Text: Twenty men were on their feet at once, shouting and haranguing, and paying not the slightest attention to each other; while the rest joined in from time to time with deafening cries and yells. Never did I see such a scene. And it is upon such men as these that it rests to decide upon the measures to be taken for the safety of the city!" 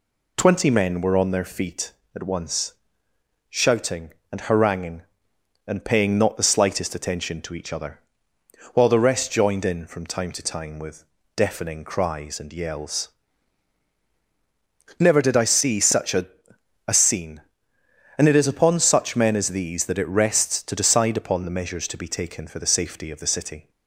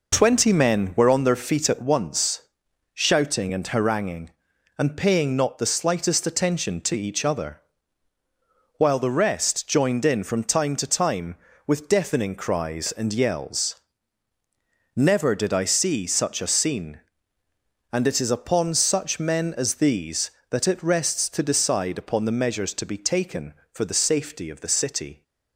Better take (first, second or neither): second